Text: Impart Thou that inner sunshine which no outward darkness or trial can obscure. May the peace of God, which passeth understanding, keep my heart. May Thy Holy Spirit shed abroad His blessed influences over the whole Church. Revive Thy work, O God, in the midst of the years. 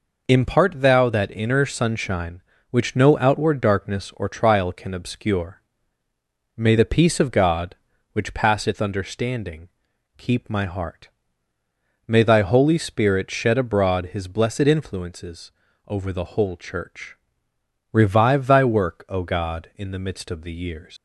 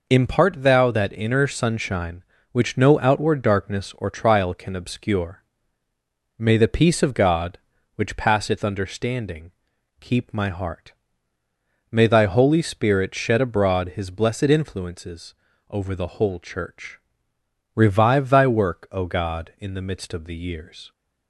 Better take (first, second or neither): second